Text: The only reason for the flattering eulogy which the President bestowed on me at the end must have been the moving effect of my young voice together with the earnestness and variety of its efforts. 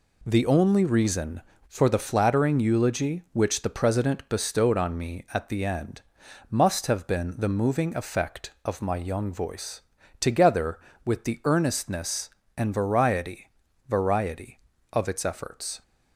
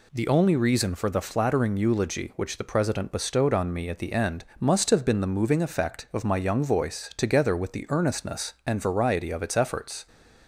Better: second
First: pauses between "end" and "must"; noticeable; at 6.0 s; 0.48 s long // pauses between "voice" and "together"; at 9.8 s; 0.40 s long // says "variety" twice; at 13.8 s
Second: pauses between "end" and "must"; slight; at 4.4 s; 0.16 s long

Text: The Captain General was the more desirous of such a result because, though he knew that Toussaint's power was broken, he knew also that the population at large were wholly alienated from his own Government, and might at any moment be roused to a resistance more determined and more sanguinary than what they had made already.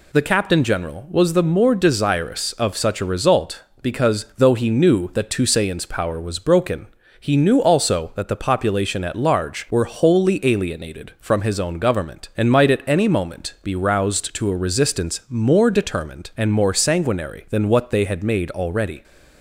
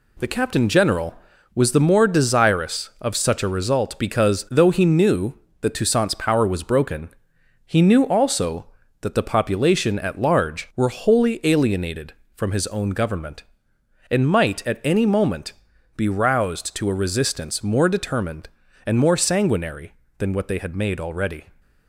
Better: first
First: none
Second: gets quieter; noticeable; throughout; 5.5 dB // pauses between "moment" and "be"; at 15.5 s; 0.44 s long

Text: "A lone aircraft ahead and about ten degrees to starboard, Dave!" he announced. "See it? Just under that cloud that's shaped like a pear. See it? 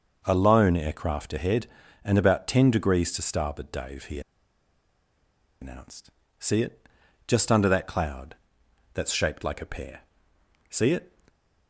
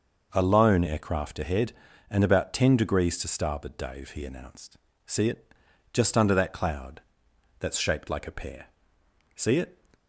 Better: second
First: pauses between "he" and "announced"; strong; at 4.2 s; 1.4 s long // pauses between "cloud" and "that's"; noticeable; at 8.3 s; 0.58 s long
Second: pauses between "cloud" and "that's"; noticeable; at 7.0 s; 0.58 s long

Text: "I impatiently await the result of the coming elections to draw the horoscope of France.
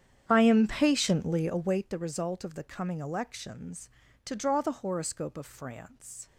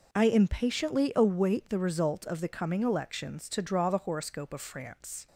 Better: second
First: starts louder than the rest; strong; until 1.9 s; 9 dB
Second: none

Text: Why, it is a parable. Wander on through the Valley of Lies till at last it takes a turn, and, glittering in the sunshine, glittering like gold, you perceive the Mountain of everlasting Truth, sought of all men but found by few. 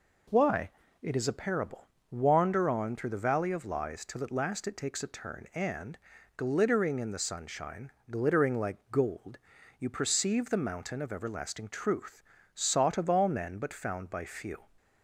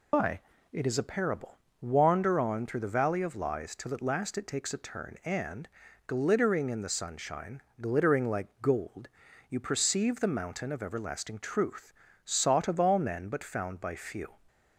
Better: first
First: none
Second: loses the start of "Why"; at 0.1 s; 155 ms

